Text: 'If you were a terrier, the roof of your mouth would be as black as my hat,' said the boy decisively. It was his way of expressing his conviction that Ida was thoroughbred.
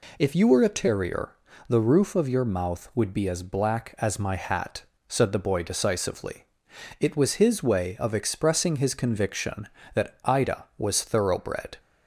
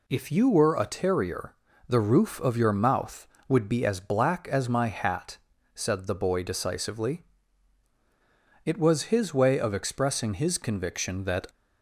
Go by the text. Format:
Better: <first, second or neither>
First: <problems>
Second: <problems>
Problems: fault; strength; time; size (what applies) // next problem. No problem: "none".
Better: first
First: none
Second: stops before "Ida was thoroughbred"; at 11.4 s